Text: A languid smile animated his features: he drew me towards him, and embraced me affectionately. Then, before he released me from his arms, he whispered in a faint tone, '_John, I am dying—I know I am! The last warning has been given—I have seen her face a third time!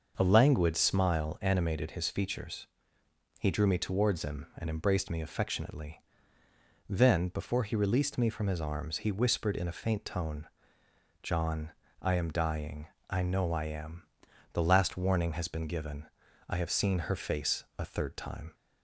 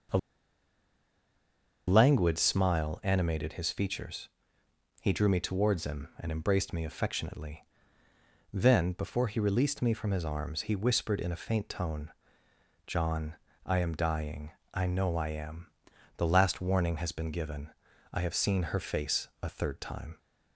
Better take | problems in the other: first | starts louder than the rest; noticeable; until 2.8 s; 6 dB; noticeable in the first // pauses between "A" and "languid"; strong; at 0.1 s; 1.6 s long

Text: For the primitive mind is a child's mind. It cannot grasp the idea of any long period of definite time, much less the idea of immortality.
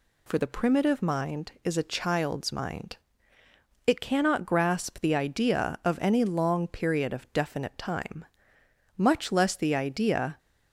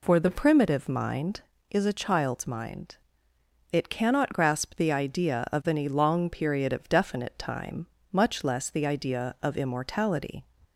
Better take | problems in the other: second | stops before "of immortality"; at 10.3 s

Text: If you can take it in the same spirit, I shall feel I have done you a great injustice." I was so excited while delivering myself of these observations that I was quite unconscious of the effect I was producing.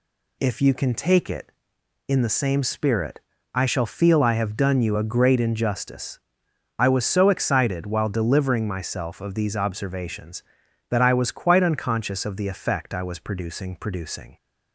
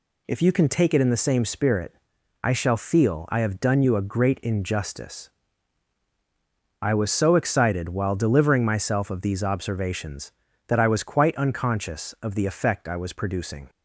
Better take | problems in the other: second | says "producing" twice; at 13.7 s

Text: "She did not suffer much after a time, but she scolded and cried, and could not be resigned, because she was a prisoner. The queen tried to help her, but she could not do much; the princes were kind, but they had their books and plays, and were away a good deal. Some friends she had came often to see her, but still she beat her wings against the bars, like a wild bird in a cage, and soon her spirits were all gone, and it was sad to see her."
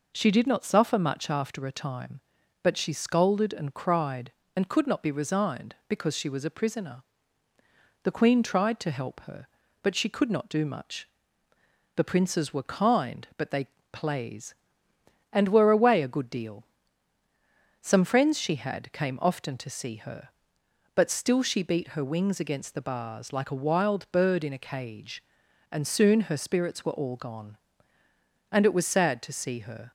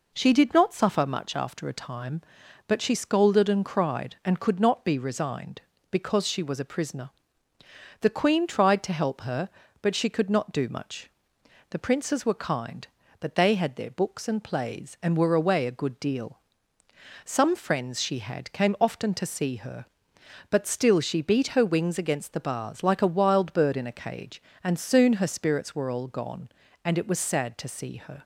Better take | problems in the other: second | skips "had their books and"; at 13.7 s

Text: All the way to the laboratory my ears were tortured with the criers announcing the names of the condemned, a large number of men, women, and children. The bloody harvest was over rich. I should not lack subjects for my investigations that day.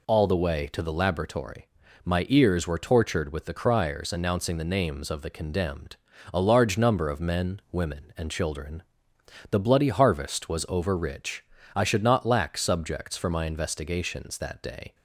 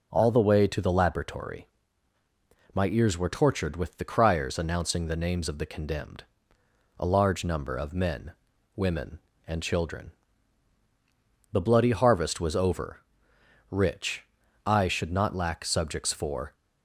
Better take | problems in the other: first | pauses between "laboratory" and "my"; at 1.6 s; 1.0 s long; slight in the first // pauses between "over" and "rich"; noticeable; at 13.0 s; 0.72 s long // stops before "my investigations that day"; at 16.5 s

